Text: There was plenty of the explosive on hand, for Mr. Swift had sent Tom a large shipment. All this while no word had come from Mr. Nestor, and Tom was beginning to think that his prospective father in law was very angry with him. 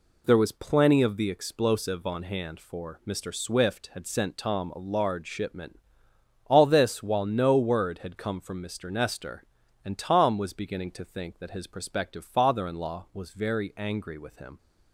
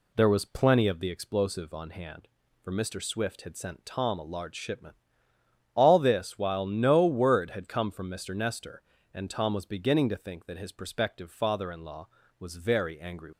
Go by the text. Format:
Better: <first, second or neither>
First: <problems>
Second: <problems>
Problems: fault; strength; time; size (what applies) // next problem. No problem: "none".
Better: first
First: none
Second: stops before "with him"; at 13.3 s